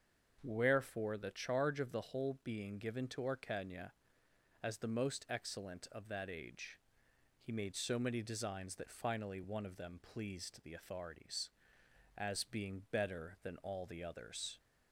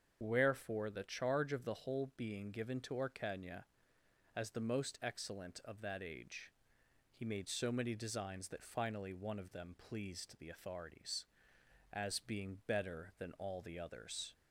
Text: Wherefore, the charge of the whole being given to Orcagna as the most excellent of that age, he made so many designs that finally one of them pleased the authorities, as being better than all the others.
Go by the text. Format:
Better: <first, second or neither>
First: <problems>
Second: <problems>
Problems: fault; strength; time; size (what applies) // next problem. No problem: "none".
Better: first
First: starts louder than the rest; until 1.4 s; 6.5 dB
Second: loses the start of "Wherefore"; at 0.2 s; 95 ms // starts louder than the rest; until 1.2 s; 7 dB